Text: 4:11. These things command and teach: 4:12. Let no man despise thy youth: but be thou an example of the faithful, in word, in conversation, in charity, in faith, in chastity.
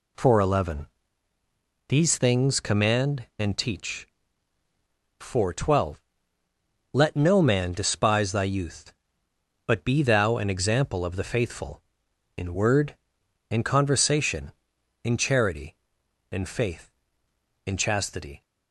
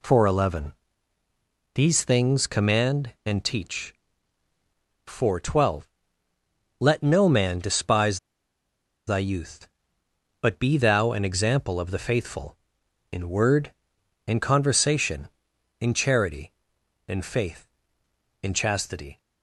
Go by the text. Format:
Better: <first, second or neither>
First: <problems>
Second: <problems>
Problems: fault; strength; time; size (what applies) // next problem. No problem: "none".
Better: first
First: none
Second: pauses between "despise" and "thy"; noticeable; at 8.1 s; 0.89 s long